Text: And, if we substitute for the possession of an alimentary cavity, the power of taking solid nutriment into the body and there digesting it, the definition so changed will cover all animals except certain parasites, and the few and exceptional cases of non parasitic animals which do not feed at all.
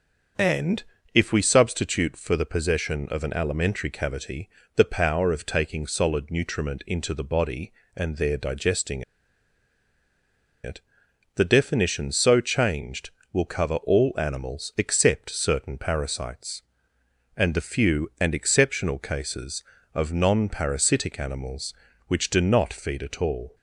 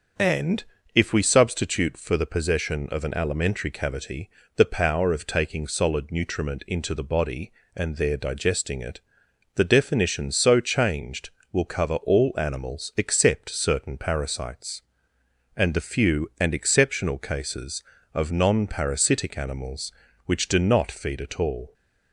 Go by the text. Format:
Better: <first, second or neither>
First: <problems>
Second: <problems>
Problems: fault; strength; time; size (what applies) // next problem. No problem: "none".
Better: second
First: starts louder than the rest; until 1.6 s; 6.5 dB // pauses between "digesting" and "it"; strong; at 9.0 s; 1.6 s long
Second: starts louder than the rest; until 1.4 s; 6.5 dB